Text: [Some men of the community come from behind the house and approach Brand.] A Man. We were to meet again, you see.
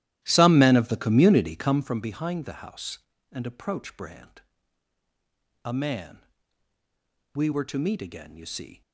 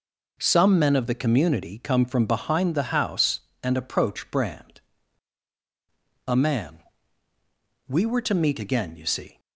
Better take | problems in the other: second | starts louder than the rest; strong; until 1.9 s; 13.5 dB

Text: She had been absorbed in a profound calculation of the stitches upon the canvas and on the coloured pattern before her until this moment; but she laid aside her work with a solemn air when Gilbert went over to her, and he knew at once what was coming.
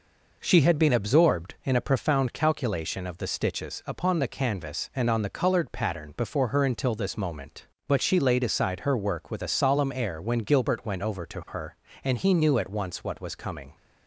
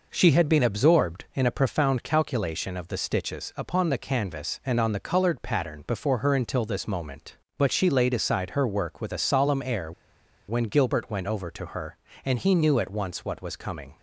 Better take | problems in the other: first | pauses between "air" and "when"; noticeable; at 9.9 s; 0.56 s long

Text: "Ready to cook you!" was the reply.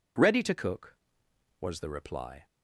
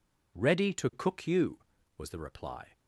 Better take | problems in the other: second | skips "you"; at 1.2 s

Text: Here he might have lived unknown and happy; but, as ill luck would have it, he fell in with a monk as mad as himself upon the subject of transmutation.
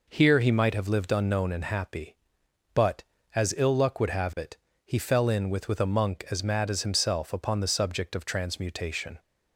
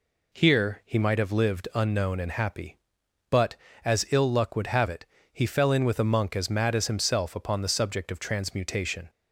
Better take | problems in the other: second | says "with" twice; at 5.6 s

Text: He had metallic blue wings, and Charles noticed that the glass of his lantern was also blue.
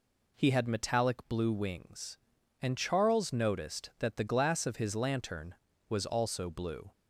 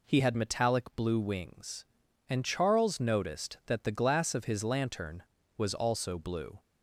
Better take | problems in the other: neither | none

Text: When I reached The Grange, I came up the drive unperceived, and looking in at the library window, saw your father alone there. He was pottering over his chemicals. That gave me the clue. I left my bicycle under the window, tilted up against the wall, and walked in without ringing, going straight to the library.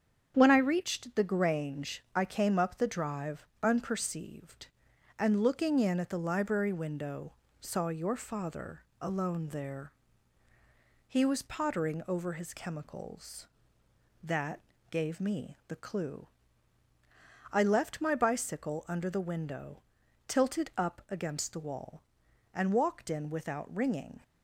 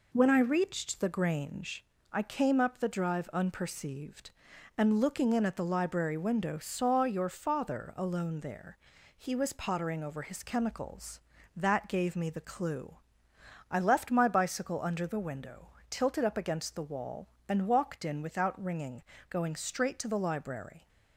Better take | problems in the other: second | starts louder than the rest; strong; until 1.3 s; 7.5 dB // pauses between "drive" and "unperceived"; slight; at 3.4 s; 0.18 s long // pauses between "father" and "alone"; slight; at 8.8 s; 0.18 s long // pauses between "That" and "gave"; slight; at 14.5 s; 0.30 s long // stops before "going straight to the library"; at 24.2 s

